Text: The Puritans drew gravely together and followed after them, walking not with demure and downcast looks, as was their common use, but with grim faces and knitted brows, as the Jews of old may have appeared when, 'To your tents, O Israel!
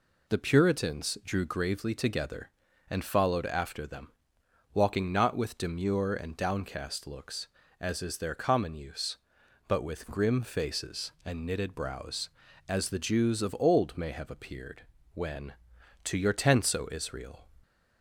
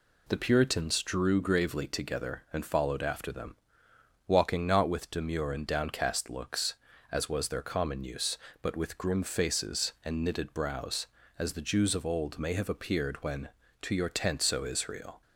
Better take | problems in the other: second | says "is" for "was"; at 8.0 s // pauses between "appeared" and "when"; slight; at 14.8 s; 0.30 s long

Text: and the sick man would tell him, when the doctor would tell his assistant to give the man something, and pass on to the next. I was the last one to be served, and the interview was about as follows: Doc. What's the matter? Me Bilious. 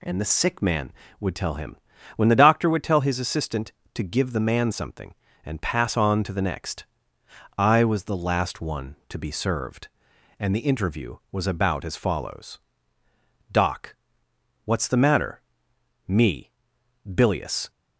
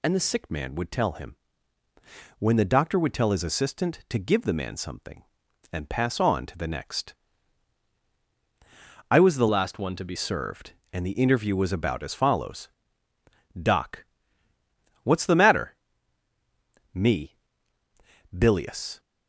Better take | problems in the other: first | changes voice from "last" to "be"; from 9.4 to 10.1 s; 0.7 s long // pauses between "Me" and "Bilious"; noticeable; at 17.3 s; 0.96 s long; noticeable in the first

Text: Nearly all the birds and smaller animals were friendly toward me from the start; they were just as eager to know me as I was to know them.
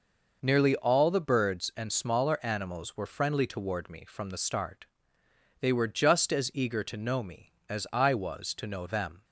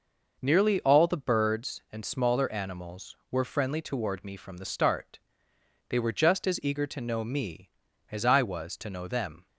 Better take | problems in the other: neither | none

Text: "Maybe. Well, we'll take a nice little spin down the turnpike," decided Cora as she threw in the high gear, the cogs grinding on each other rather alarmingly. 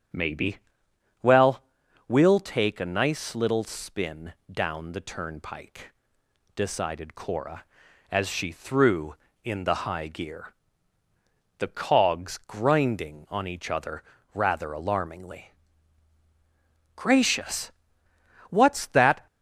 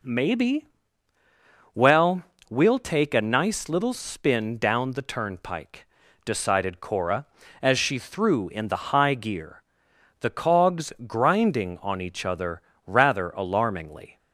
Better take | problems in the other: second | starts louder than the rest; strong; until 2.1 s; 8.5 dB // pauses between "spin" and "down"; slight; at 4.3 s; 0.16 s long // pauses between "other" and "rather"; slight; at 14.0 s; 0.30 s long; slight in the second // goes on to say "Gracious What's that"; strong; from 16.9 s on; 2.3 s long

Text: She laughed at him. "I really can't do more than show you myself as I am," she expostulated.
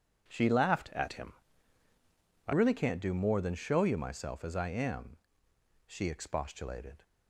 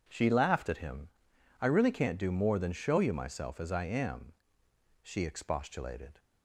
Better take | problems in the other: second | changes voice from "at" to "I"; from 0.9 to 2.5 s; 1.6 s long

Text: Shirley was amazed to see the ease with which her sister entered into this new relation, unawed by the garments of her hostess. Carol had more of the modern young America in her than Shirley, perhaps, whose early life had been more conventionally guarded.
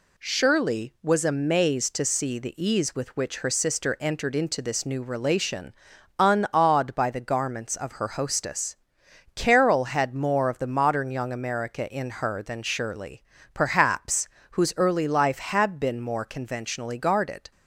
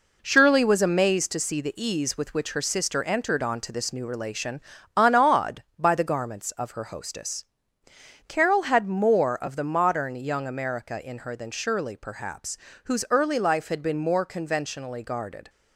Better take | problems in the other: first | says "onto" for "into"; at 3.4 s

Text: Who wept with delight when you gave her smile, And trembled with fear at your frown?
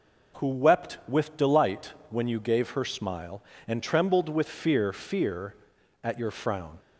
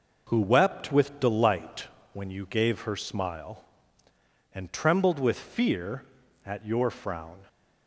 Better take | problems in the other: second | pauses between "delight" and "when"; slight; at 1.9 s; 0.16 s long; slight in the second // says "fear" twice; at 4.9 s

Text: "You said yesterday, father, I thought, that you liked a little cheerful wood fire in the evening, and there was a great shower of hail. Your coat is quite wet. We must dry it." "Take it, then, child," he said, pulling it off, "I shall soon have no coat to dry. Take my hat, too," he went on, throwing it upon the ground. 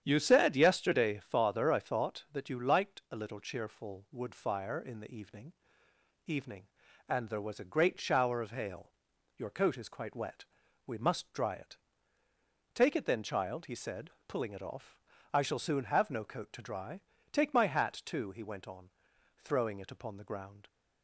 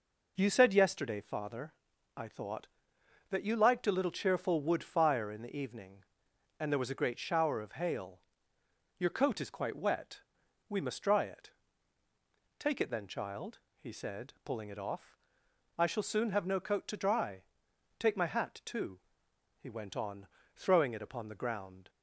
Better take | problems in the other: second | starts louder than the rest; strong; until 1.0 s; 9 dB // says "evening" twice; at 6.2 s

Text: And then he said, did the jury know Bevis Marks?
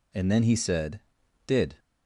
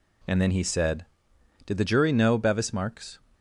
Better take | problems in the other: second | stops before "the jury know Bevis Marks"; at 1.7 s

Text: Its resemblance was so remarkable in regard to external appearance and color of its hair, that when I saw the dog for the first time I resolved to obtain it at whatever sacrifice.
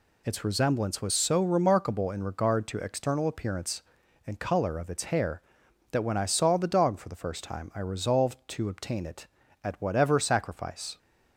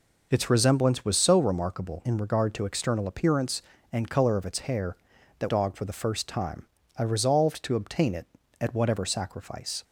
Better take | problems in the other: first | skips "when I saw the"; at 5.4 s // pauses between "time" and "I"; slight; at 6.6 s; 0.34 s long

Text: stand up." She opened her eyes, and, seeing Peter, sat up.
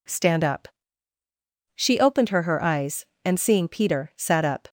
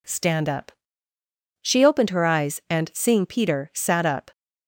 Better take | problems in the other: second | says "her" twice; at 2.4 s

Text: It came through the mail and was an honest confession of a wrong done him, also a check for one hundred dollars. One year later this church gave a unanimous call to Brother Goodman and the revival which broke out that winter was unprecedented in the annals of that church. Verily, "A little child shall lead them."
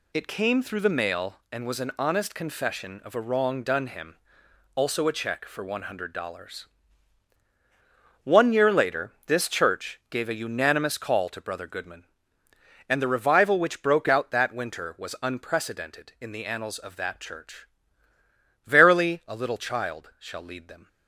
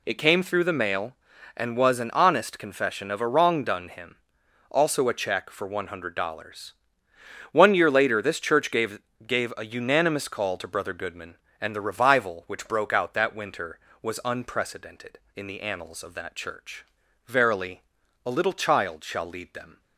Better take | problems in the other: first | says "gave" twice; at 9.2 s

